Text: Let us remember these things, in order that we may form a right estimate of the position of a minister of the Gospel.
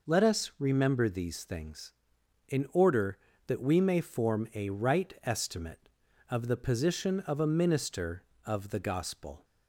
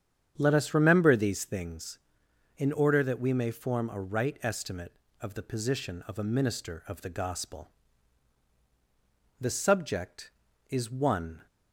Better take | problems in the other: first | starts louder than the rest; strong; until 1.3 s; 8.5 dB // goes on to say "The subject is one"; strong; from 9.3 s on; 2.0 s long

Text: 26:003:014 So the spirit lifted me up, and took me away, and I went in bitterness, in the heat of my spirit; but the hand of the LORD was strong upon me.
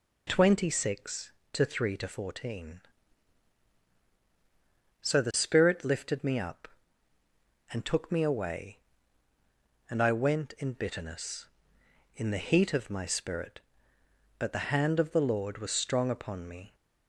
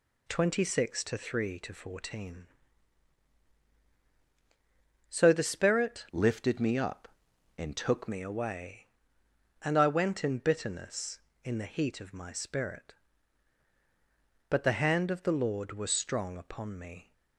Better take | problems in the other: first | changes voice from "lifted" to "took"; from 6.1 to 8.0 s; 1.9 s long

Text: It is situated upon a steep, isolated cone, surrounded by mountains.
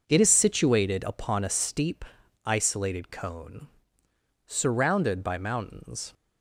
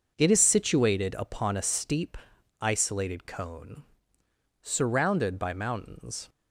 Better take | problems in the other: neither | none

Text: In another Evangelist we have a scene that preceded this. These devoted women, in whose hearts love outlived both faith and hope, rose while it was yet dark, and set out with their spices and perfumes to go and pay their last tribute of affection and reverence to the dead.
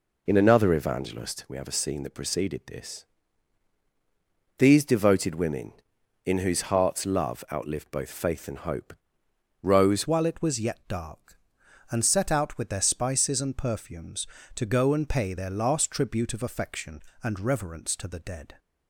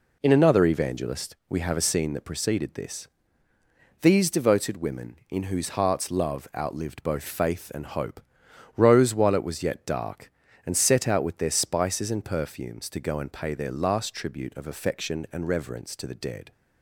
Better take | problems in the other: second | changes voice at "while"; from 10.0 s on; 8.5 s long

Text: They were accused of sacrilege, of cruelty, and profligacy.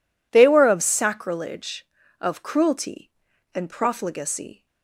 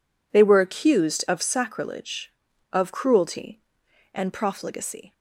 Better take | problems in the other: second | skips "accused"; at 0.6 s

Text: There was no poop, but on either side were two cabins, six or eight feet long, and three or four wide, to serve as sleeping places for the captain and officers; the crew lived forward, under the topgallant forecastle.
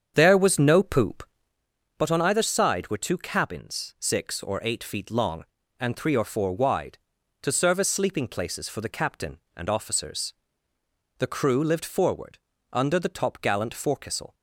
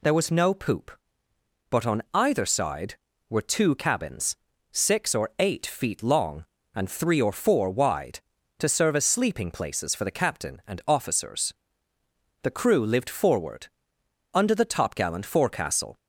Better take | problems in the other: second | starts louder than the rest; strong; until 1.6 s; 7.5 dB

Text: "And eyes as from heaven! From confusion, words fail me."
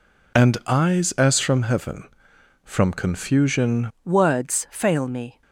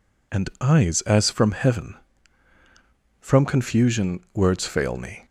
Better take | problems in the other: second | changes voice at "words"; from 4.0 s on; 1.4 s long

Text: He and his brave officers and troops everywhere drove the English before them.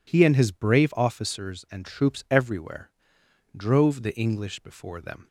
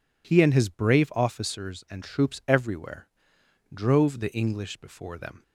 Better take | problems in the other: neither | pauses between "everywhere" and "drove"; noticeable; the same in both

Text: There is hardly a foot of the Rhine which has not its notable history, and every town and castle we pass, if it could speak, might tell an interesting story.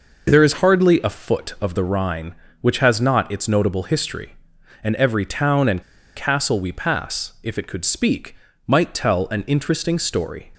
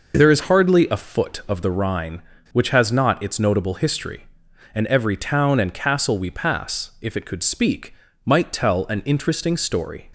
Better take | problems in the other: second | pauses between "and" and "castle"; slight; at 5.8 s; 0.33 s long

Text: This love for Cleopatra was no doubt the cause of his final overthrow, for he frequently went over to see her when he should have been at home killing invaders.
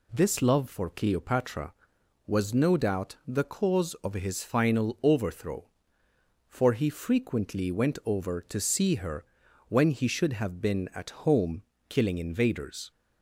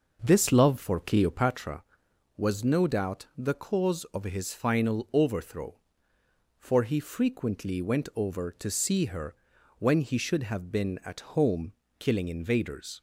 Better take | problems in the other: first | starts louder than the rest; noticeable; until 1.6 s; 6 dB // pauses between "her" and "when"; at 9.3 s; 0.44 s long; also in the first // pauses between "home" and "killing"; slight; at 11.7 s; 0.26 s long; slight in the first

